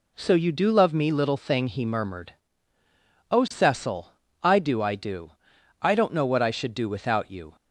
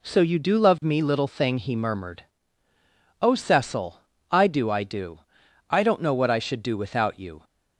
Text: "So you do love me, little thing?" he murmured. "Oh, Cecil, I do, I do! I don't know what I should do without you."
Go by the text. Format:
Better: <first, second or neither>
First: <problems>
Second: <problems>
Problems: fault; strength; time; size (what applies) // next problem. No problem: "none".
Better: neither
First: none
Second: none